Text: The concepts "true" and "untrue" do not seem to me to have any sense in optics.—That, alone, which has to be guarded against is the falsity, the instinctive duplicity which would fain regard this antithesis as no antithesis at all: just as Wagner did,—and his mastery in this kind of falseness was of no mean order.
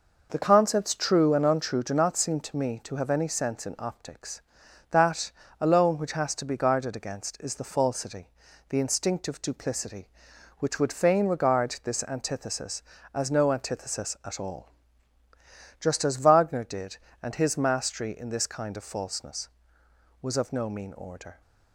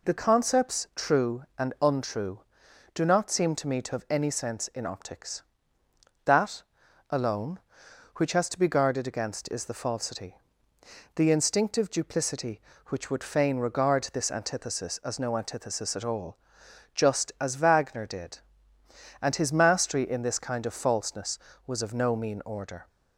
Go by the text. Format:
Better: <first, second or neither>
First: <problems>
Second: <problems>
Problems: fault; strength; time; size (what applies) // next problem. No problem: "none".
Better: neither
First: none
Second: none